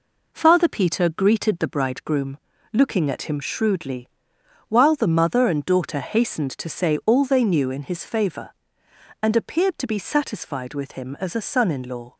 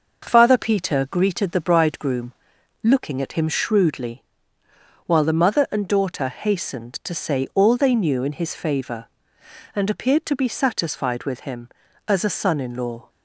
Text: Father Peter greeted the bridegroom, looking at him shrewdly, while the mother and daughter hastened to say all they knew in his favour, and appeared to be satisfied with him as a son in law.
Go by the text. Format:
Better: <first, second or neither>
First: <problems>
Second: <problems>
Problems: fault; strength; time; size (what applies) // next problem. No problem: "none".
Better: neither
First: none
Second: none